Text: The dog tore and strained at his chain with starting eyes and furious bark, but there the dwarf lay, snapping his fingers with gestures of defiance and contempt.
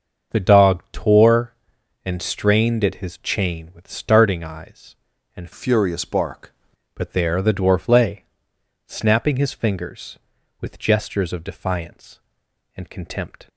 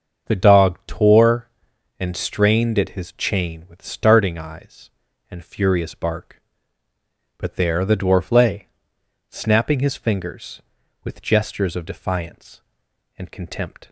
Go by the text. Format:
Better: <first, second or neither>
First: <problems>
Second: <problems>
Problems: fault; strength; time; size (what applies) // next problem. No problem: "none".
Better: second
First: starts louder than the rest; until 1.4 s; 6.5 dB // changes voice from "furious" to "bark"; from 5.5 to 6.5 s; 1.0 s long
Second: starts louder than the rest; until 1.3 s; 7 dB